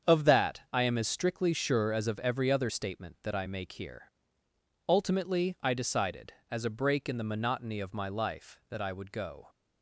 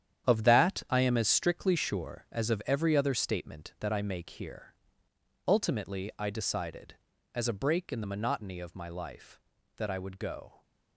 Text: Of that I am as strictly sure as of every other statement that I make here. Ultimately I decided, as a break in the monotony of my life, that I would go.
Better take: first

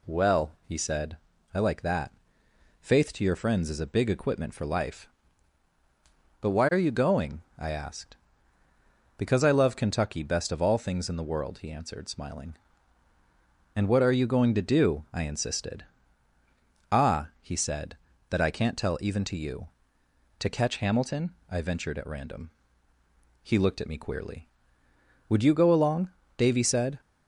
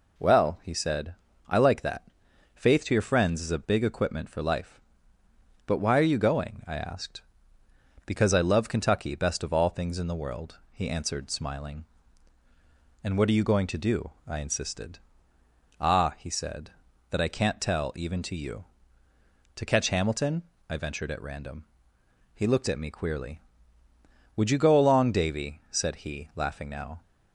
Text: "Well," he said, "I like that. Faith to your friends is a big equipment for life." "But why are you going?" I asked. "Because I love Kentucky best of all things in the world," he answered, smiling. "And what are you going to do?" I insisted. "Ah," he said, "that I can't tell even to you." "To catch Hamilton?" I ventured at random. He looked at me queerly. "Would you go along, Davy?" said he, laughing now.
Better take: second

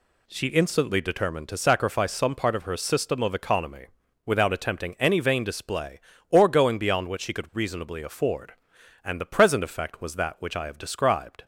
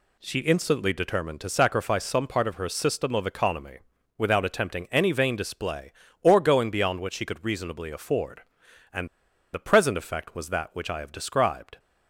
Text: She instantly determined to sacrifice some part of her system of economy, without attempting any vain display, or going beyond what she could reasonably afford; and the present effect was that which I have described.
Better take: first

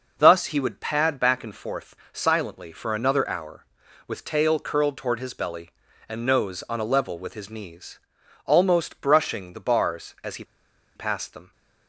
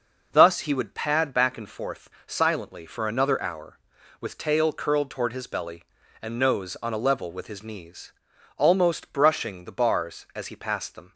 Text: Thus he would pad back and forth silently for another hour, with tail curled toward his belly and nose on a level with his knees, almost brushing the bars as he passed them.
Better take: second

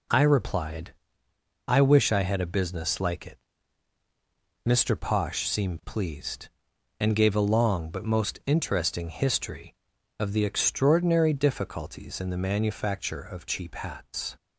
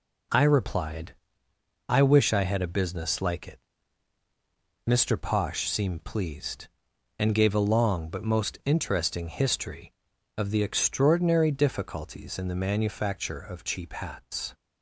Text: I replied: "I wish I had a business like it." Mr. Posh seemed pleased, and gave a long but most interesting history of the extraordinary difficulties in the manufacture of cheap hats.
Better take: neither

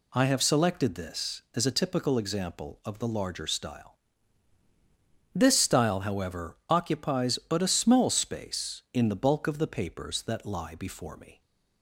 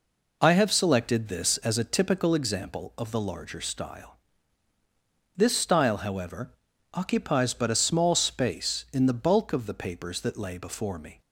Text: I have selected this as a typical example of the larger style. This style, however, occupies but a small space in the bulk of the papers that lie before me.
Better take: first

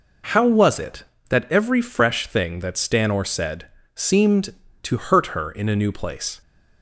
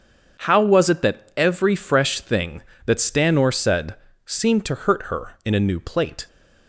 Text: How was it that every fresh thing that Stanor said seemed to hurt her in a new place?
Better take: first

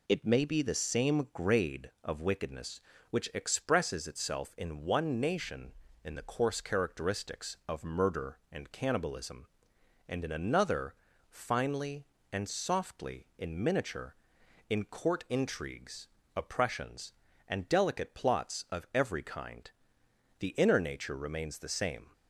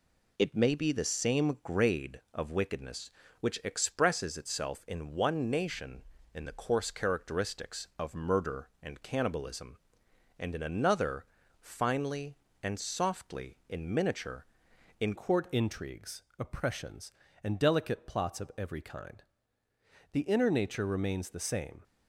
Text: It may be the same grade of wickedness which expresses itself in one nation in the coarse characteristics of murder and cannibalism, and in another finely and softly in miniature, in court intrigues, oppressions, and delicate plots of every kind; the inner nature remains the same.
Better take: first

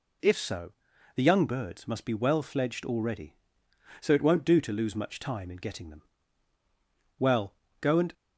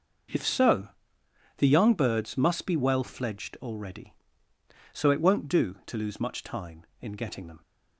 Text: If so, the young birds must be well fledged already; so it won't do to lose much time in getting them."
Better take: second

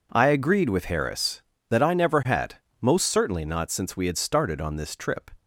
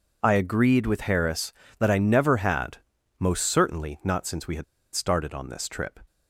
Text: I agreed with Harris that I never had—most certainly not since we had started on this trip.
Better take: first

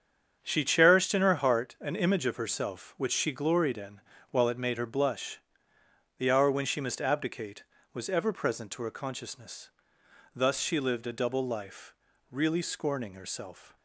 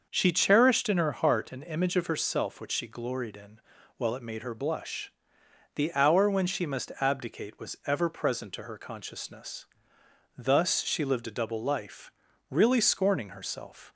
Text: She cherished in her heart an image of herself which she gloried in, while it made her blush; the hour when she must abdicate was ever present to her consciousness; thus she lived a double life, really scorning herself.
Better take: neither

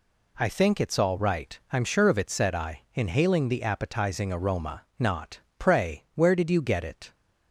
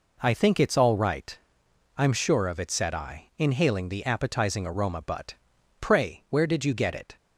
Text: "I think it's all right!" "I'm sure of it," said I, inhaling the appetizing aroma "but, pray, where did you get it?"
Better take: second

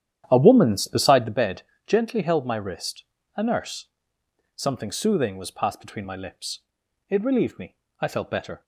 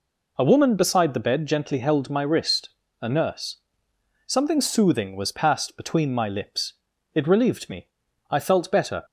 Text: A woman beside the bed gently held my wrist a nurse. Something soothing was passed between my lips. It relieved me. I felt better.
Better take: second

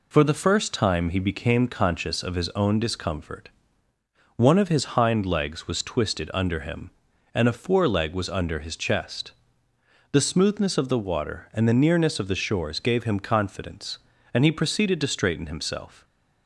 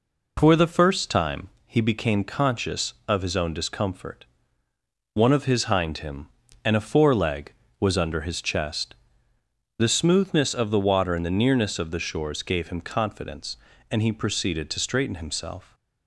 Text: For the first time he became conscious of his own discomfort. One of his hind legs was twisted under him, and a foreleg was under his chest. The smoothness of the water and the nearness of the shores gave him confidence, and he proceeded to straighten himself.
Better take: first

